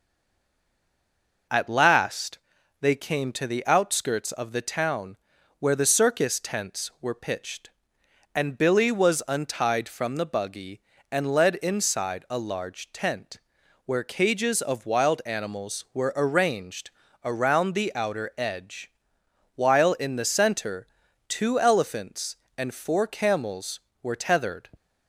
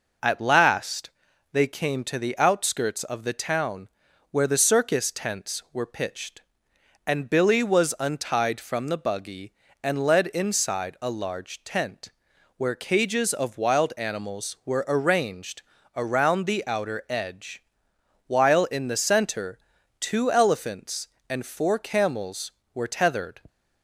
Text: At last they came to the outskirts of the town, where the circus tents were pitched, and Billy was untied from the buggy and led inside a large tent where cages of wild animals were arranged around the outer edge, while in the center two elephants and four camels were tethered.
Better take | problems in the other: second | stays silent before the first word; noticeable; until 1.4 s; 1.4 s long // pauses between "last" and "they"; at 2.3 s; 0.42 s long; also in the second // pauses between "tent" and "where"; noticeable; at 13.3 s; 0.48 s long; noticeable in the second // pauses between "arranged" and "around"; slight; at 16.8 s; 0.34 s long; slight in the second // pauses between "center" and "two"; at 20.8 s; 0.40 s long; also in the second

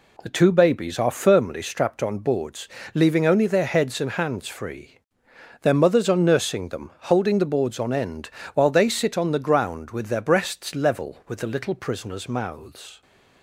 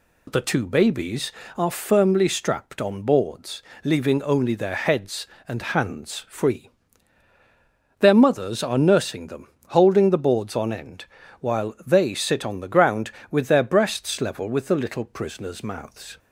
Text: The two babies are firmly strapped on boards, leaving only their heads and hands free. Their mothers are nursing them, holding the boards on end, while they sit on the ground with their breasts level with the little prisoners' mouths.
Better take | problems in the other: neither | none

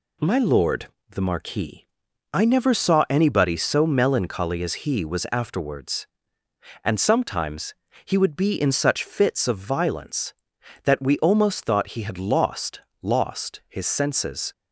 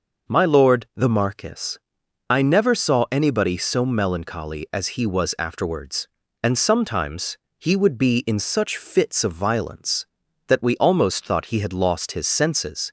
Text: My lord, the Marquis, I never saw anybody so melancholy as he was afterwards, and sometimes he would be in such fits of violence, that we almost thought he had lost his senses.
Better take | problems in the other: second | pauses between "sometimes" and "he"; slight; at 7.7 s; 0.30 s long; slight in the second // says "lost" twice; at 13.0 s

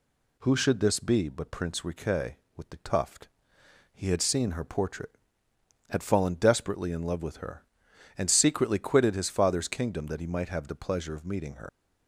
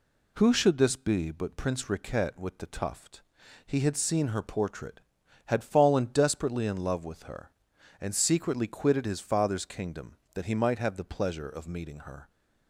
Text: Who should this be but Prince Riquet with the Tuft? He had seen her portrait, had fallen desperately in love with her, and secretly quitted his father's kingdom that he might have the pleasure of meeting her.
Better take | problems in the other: second | leaves "her" unfinished; at 11.6 s; 85 ms

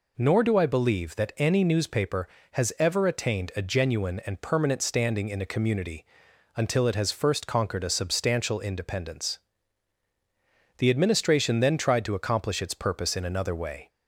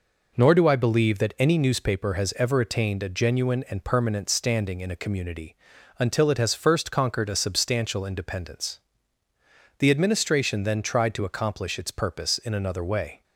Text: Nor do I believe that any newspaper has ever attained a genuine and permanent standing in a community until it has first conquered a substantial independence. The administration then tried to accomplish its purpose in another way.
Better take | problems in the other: neither | pauses between "community" and "until"; the same in both

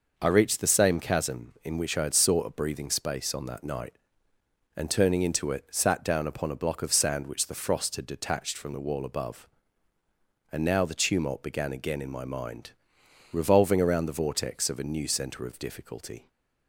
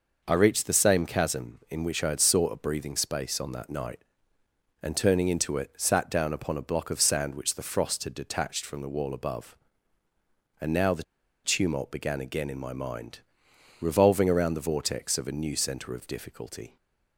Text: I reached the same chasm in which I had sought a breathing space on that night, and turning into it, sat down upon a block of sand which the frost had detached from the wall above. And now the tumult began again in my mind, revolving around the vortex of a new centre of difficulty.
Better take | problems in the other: first | pauses between "the" and "tumult"; at 11.0 s; 0.41 s long

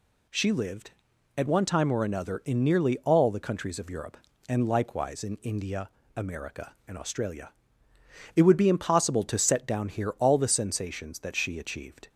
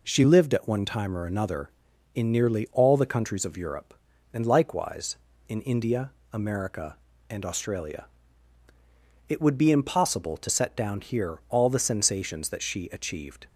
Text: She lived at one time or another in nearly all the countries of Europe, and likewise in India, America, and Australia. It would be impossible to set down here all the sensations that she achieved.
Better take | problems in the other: neither | none

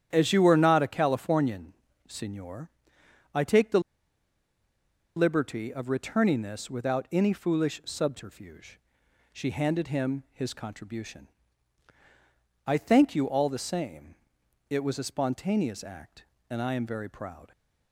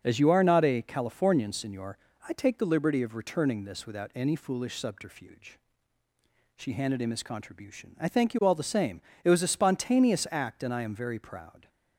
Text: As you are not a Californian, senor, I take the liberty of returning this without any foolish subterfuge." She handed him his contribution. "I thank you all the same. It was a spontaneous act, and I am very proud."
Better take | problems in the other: second | starts louder than the rest; strong; until 1.1 s; 10 dB; also in the second // pauses between "the" and "liberty"; strong; at 3.7 s; 1.3 s long

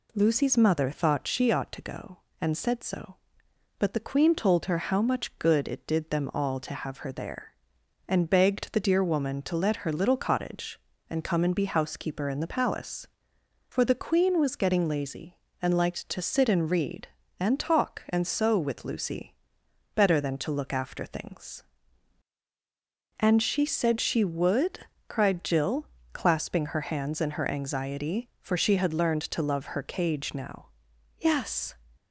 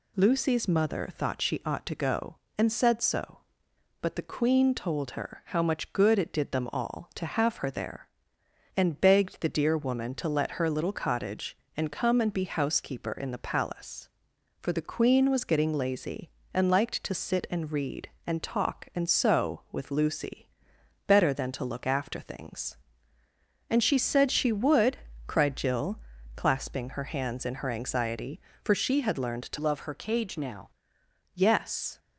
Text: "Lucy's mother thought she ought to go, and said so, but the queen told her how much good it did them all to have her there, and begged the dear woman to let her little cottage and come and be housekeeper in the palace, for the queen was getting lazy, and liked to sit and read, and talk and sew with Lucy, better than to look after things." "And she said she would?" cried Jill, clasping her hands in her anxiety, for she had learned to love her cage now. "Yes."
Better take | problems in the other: first | changes voice from "love" to "now"; from 29.5 to 30.6 s; 1.1 s long

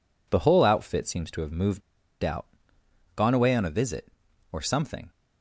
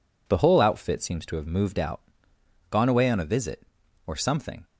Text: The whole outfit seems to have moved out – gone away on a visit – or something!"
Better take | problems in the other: second | pauses between "moved" and "out"; at 1.8 s; 0.43 s long

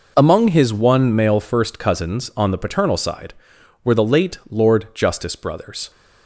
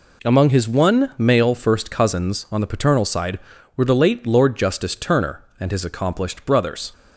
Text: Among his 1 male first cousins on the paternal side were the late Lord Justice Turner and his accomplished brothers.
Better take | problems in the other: second | skips "Turner and his accomplished"; at 5.3 s

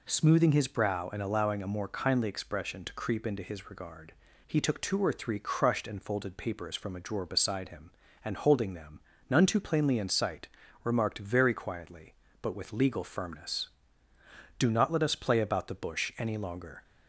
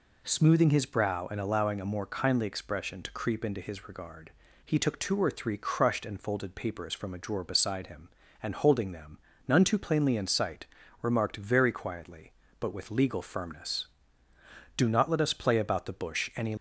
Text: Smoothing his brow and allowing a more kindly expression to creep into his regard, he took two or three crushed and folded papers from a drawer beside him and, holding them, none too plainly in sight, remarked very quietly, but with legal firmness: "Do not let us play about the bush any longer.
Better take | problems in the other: first | stops before "longer"; at 16.5 s

